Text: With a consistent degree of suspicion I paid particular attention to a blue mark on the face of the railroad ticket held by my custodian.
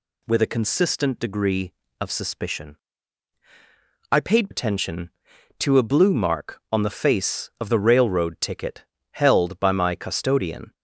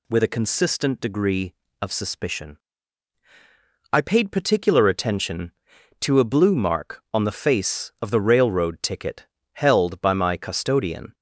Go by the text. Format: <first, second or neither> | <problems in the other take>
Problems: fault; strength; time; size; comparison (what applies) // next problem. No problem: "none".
second | pauses between "suspicion" and "I"; strong; at 2.7 s; 1.3 s long; strong in the second // skips "particular"; at 4.5 s // pauses between "ticket" and "held"; slight; at 8.8 s; 0.28 s long; slight in the second